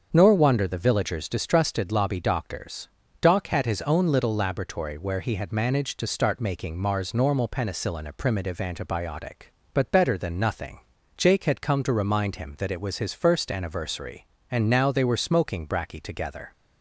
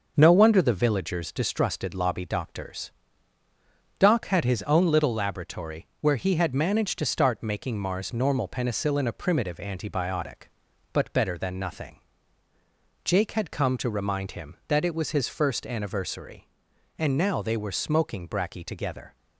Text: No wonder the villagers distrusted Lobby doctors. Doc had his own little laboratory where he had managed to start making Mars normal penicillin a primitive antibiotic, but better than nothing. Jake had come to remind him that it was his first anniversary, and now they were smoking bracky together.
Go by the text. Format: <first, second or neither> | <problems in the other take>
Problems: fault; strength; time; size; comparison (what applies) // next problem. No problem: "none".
second | starts louder than the rest; until 1.1 s; 7 dB // says "Nor" for "No"; at 0.1 s